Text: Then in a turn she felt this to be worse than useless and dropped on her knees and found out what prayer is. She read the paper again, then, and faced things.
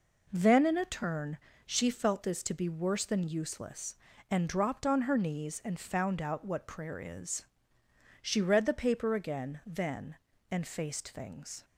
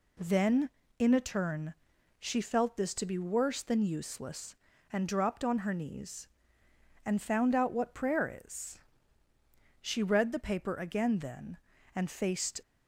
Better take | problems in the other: first | pauses between "turn" and "she"; at 1.7 s; 0.44 s long; slight in the first // stops before "things"; at 12.6 s

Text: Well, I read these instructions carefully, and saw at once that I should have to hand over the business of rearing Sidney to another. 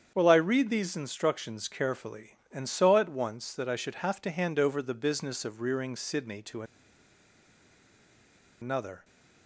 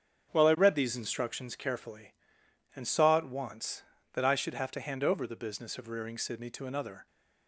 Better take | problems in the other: second | starts louder than the rest; strong; until 1.1 s; 8 dB; strong in the second // pauses between "to" and "another"; strong; at 6.6 s; 1.9 s long

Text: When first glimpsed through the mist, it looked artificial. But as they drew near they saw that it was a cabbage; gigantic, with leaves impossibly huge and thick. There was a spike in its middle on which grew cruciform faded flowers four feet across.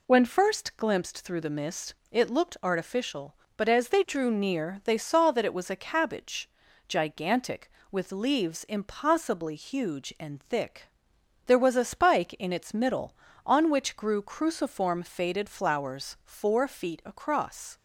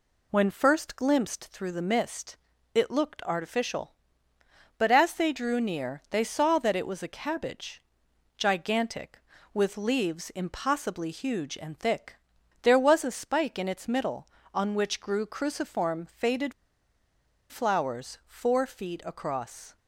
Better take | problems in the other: first | pauses between "faded" and "flowers"; noticeable; at 16.5 s; 0.97 s long

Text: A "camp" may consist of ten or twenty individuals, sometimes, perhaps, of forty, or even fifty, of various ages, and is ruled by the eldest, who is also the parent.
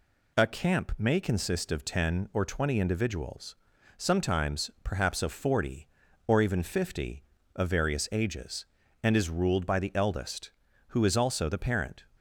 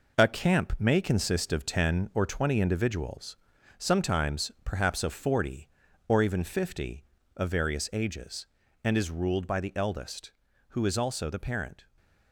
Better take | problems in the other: first | gets quieter; throughout; 6.5 dB

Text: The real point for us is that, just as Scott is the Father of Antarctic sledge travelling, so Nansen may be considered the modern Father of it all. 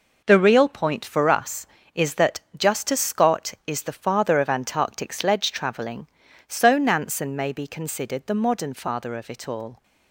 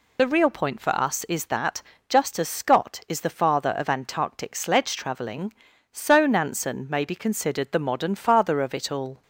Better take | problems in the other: first | loses the start of "The"; at 0.1 s; 30 ms

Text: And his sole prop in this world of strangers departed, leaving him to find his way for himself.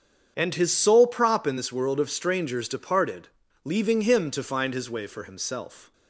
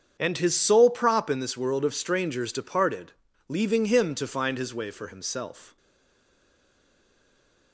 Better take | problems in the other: first | starts louder than the rest; strong; until 1.2 s; 7.5 dB; strong in the first // stays silent after the last word; noticeable; from 5.7 s on; 2.0 s long

